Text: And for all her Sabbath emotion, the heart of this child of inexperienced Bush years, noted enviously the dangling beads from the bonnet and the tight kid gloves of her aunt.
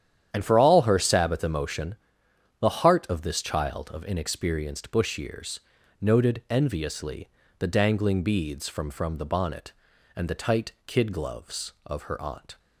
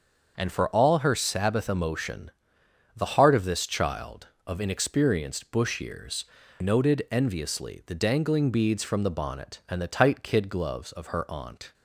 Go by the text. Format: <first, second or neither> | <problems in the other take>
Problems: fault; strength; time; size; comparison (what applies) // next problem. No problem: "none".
second | starts louder than the rest; strong; until 1.3 s; 10 dB; also in the second // pauses between "enviously" and "the"; slight; at 7.2 s; 0.31 s long // says "from" twice; at 8.8 s